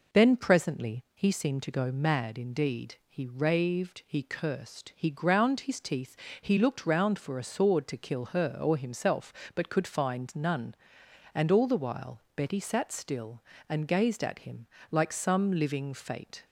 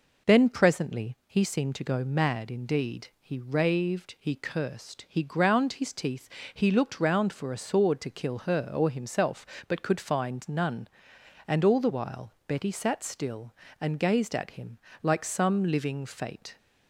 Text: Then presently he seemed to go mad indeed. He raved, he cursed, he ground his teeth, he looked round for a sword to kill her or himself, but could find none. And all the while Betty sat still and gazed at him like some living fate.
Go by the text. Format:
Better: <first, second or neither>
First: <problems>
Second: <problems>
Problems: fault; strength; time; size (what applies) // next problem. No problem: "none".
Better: neither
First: pauses between "him" and "like"; slight; at 14.6 s; 0.26 s long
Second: pauses between "him" and "like"; slight; at 14.7 s; 0.26 s long